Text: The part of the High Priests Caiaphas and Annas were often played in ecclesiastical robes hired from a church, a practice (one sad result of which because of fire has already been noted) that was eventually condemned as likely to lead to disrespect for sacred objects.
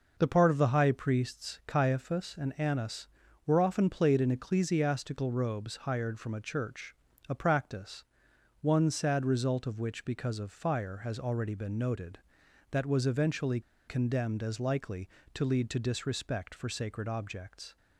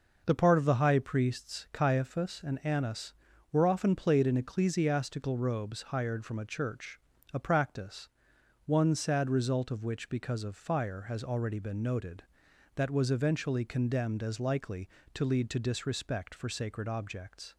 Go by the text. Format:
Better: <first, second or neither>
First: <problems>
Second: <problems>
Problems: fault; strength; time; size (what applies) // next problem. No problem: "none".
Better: second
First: pauses between "eventually" and "condemned"; slight; at 13.5 s; 0.27 s long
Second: none